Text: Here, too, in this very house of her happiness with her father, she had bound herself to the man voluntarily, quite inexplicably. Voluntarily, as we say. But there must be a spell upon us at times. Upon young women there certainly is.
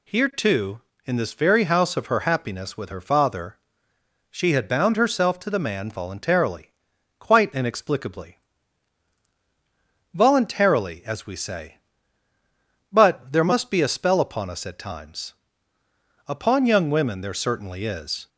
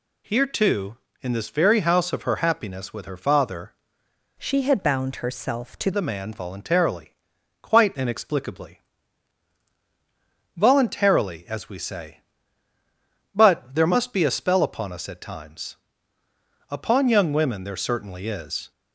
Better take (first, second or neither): first